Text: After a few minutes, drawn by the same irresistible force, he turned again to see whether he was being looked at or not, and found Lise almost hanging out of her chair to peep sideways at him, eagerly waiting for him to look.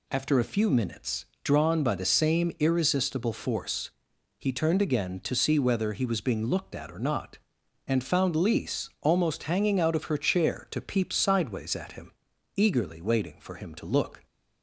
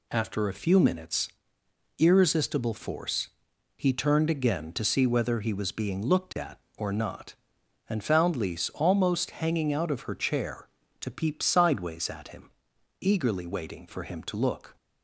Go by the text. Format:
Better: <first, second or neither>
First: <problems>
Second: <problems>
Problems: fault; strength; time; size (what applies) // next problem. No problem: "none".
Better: first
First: none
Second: skips "drawn by the same"; at 1.6 s